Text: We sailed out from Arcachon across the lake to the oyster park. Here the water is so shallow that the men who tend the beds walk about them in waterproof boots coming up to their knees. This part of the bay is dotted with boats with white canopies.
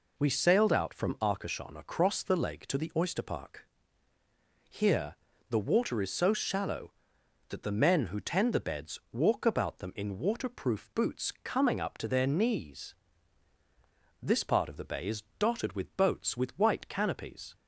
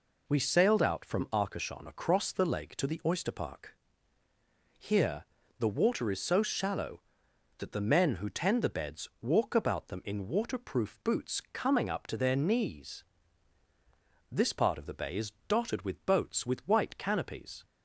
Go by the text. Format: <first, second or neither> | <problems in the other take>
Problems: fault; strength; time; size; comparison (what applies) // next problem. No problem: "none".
neither | pauses between "Here" and "the"; slight; the same in both // pauses between "is" and "dotted"; slight; the same in both